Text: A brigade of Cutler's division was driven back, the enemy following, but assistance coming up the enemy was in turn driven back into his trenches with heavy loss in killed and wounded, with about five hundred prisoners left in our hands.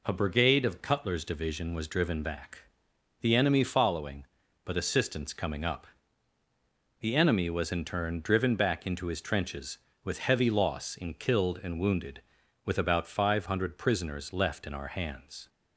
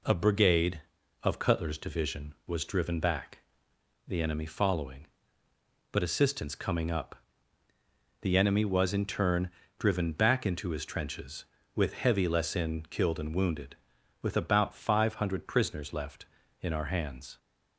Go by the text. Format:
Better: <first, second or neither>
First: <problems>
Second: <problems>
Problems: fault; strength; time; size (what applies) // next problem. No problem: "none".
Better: first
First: pauses between "up" and "the"; at 5.8 s; 1.1 s long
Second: pauses between "up" and "the"; at 7.1 s; 1.0 s long // pauses between "turn" and "driven"; slight; at 9.4 s; 0.28 s long // says "less" for "loss"; at 12.2 s